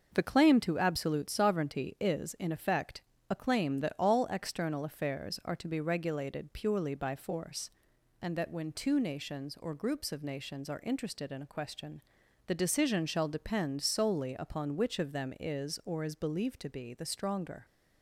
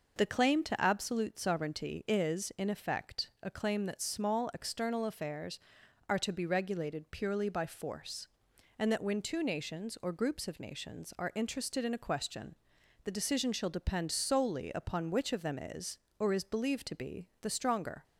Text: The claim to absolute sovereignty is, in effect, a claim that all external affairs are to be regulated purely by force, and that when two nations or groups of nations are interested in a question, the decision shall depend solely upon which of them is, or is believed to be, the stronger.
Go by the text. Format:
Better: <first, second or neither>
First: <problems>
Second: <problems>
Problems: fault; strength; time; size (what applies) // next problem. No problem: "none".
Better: first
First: none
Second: says "small" for "all"; at 4.0 s